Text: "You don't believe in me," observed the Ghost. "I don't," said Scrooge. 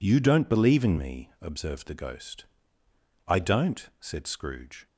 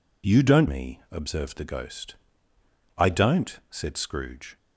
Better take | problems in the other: first | skips "believe in"; at 0.6 s

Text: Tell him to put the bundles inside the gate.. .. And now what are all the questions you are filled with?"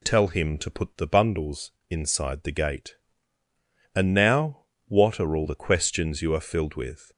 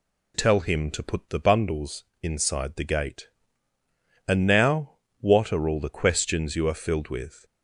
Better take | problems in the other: neither | pauses between "bundles" and "inside"; slight; the same in both // pauses between "now" and "what"; slight; the same in both

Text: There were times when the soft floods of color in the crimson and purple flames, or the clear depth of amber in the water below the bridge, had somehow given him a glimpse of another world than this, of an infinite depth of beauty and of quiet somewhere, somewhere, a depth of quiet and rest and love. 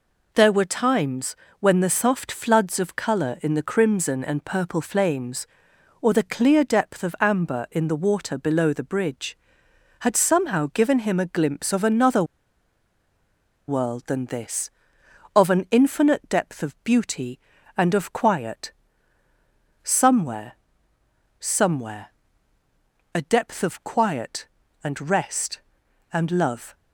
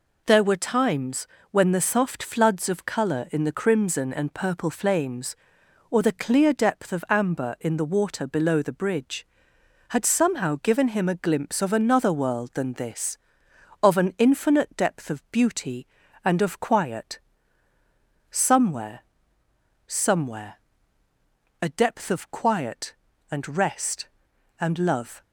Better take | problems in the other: second | pauses between "times" and "when"; slight; at 1.3 s; 0.24 s long; slight in the second // pauses between "another" and "world"; strong; at 12.2 s; 1.4 s long // pauses between "quiet" and "somewhere"; at 18.7 s; 1.1 s long; also in the second

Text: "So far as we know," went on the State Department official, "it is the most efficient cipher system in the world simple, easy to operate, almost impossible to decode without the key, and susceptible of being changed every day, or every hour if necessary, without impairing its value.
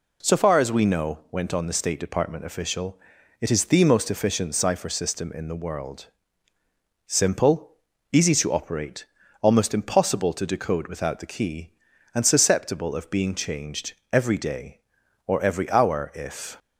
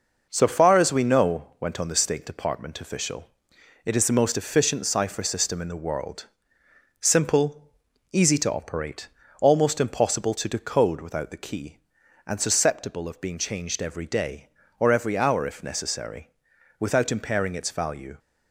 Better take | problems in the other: second | pauses between "world" and "simple"; at 6.0 s; 1.0 s long; noticeable in the second // pauses between "changed" and "every"; slight; at 13.9 s; 0.18 s long // stops before "necessary without impairing its value"; at 16.5 s

